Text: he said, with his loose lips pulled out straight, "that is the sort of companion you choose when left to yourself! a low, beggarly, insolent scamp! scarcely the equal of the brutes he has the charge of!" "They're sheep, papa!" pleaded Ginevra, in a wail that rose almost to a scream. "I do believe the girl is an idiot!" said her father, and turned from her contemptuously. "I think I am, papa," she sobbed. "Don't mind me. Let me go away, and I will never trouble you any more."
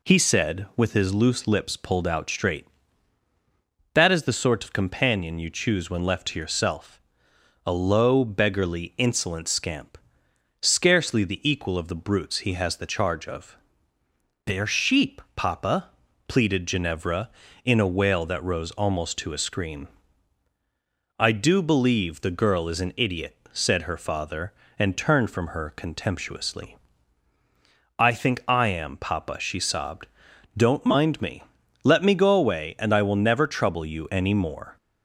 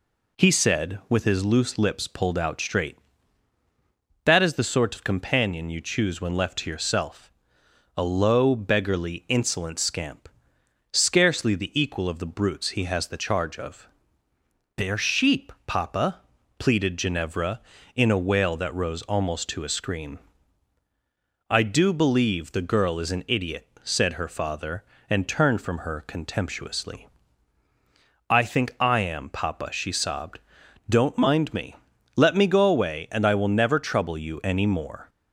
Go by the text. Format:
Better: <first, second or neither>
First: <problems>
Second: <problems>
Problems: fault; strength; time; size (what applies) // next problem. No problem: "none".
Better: neither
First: none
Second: none